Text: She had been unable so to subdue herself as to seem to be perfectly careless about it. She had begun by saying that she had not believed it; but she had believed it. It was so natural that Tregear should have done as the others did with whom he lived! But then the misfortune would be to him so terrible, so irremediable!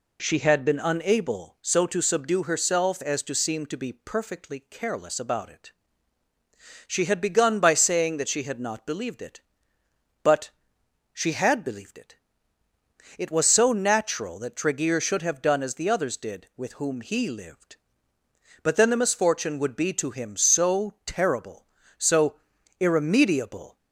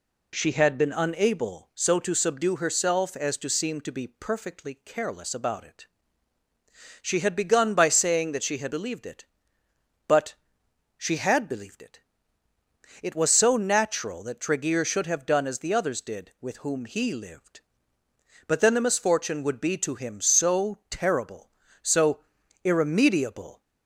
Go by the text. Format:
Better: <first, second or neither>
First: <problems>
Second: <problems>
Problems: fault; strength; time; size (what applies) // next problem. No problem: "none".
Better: first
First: pauses between "but" and "she"; noticeable; at 10.4 s; 0.64 s long // pauses between "so" and "irremediable"; at 22.3 s; 0.42 s long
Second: skips "not"; at 8.7 s // pauses between "but" and "she"; noticeable; at 10.3 s; 0.64 s long // pauses between "so" and "irremediable"; at 22.1 s; 0.42 s long